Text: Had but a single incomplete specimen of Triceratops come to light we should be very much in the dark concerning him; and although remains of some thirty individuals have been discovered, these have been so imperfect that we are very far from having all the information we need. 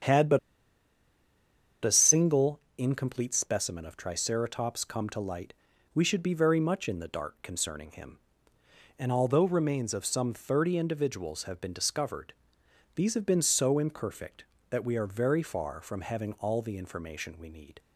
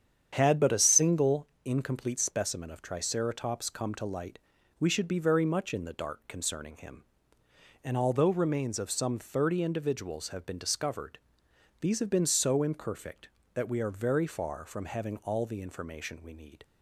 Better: second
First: starts louder than the rest; strong; until 2.4 s; 8.5 dB // pauses between "but" and "a"; strong; at 0.3 s; 1.4 s long // pauses between "single" and "incomplete"; slight; at 2.5 s; 0.18 s long // pauses between "light" and "we"; at 5.5 s; 0.42 s long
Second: starts louder than the rest; strong; until 1.3 s; 8.5 dB // pauses between "single" and "incomplete"; slight; at 1.4 s; 0.18 s long // pauses between "light" and "we"; at 4.3 s; 0.42 s long

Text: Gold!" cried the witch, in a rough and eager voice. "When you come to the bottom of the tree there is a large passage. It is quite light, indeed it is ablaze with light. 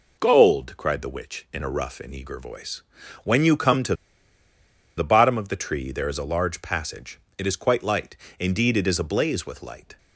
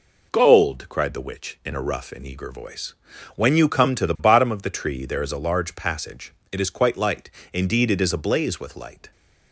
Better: second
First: pauses between "to" and "the"; at 3.9 s; 1.0 s long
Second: none

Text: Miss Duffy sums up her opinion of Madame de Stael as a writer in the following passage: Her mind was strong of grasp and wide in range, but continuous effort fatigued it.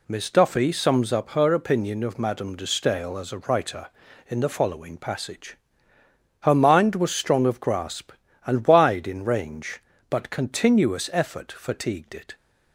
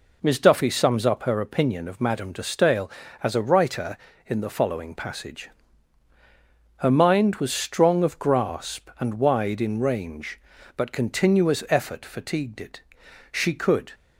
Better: first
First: none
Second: goes on to say "She could"; noticeable; from 13.3 s on; 0.62 s long

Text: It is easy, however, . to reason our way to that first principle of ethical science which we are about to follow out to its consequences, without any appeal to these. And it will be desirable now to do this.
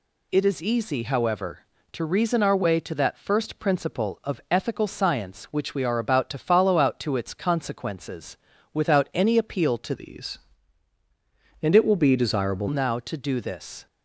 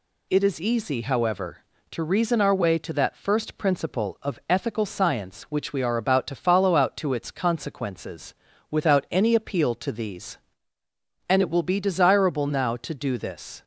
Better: second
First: changes voice from "these" to "desirable"; from 9.9 to 12.6 s; 2.7 s long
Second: none

